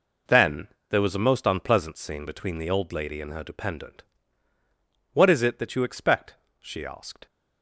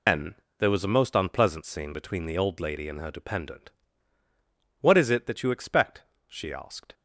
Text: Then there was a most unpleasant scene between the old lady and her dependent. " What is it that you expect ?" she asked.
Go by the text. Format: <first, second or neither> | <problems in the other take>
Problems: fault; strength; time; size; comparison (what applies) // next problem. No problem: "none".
first | loses the start of "Then"; at 0.0 s; 120 ms // pauses between "Then" and "there"; slight; at 0.3 s; 0.24 s long; slight in the first